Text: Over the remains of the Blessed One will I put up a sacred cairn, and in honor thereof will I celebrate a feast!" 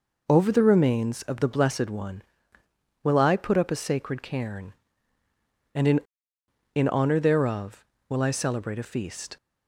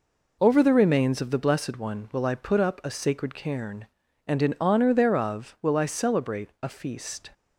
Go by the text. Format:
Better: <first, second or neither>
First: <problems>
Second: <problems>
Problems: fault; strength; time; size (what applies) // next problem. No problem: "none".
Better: second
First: says "in" twice; at 6.7 s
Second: none